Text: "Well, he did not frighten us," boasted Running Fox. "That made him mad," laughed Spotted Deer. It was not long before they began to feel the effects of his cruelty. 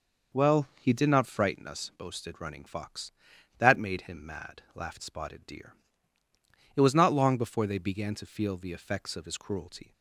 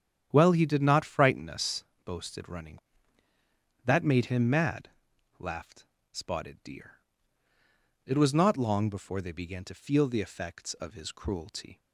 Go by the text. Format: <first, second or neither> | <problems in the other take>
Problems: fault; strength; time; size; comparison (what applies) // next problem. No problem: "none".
first | starts louder than the rest; strong; until 1.3 s; 9.5 dB // skips "Fox"; at 3.3 s // pauses between "laughed" and "Spotted"; slight; at 5.8 s; 0.26 s long